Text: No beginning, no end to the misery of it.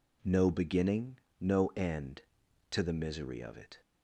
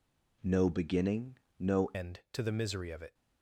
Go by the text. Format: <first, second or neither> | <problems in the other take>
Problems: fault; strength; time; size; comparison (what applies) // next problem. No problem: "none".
first | changes voice at "end"; from 1.9 s on; 1.2 s long